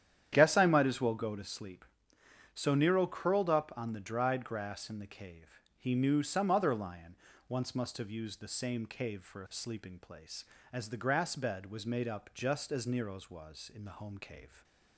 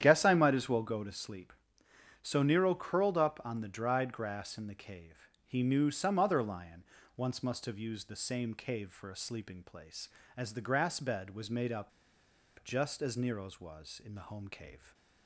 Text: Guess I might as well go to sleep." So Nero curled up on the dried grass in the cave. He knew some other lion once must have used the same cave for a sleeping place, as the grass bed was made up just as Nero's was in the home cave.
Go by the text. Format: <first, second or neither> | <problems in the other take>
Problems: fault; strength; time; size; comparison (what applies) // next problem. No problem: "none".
first | starts louder than the rest; strong; until 1.0 s; 10 dB; strong in the first // pauses between "lion" and "once"; slight; at 6.8 s; 0.32 s long; slight in the first // pauses between "up" and "just"; noticeable; at 11.9 s; 0.74 s long